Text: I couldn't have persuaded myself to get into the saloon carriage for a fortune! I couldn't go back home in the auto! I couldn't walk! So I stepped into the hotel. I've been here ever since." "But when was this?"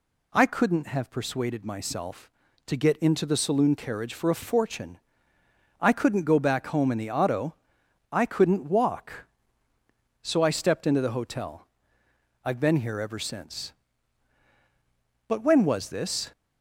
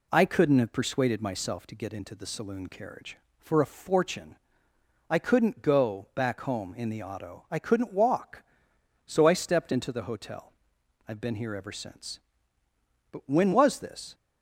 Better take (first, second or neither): neither